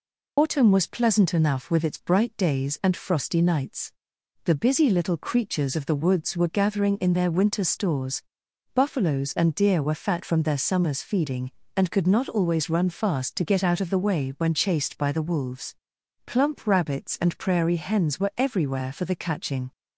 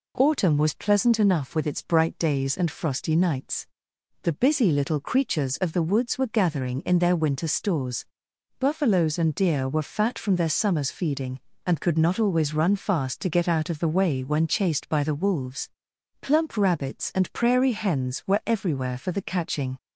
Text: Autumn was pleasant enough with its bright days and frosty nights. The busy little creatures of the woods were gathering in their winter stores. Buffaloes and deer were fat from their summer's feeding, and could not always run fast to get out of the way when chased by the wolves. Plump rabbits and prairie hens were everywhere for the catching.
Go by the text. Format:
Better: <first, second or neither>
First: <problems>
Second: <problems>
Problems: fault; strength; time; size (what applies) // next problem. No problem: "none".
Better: second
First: loses the start of "Autumn"; at 0.3 s; 70 ms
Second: none